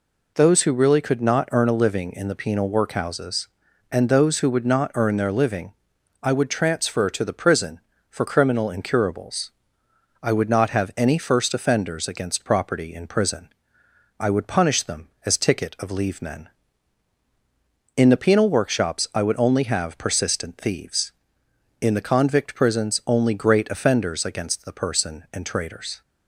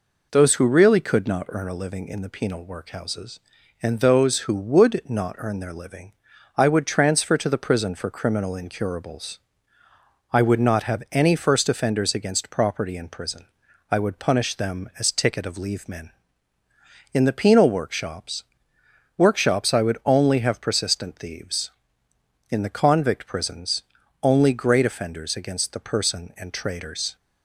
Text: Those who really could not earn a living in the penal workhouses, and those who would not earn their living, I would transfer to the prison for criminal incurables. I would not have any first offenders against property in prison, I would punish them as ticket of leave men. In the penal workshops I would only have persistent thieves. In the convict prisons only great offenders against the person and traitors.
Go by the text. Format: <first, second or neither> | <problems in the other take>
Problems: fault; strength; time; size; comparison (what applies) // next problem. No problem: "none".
first | says "workshops" twice; at 19.1 s // pauses between "prisons" and "only"; at 23.8 s; 0.40 s long